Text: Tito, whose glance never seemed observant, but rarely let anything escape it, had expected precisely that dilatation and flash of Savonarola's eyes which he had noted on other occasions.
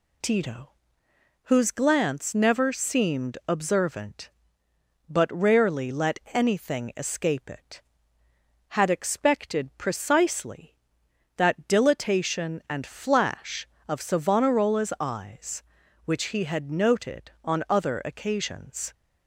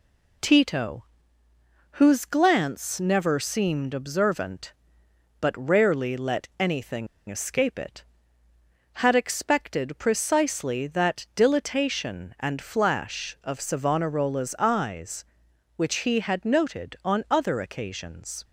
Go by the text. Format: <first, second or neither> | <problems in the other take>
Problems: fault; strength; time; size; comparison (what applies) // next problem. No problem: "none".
first | pauses between "anything" and "escape"; slight; at 7.0 s; 0.22 s long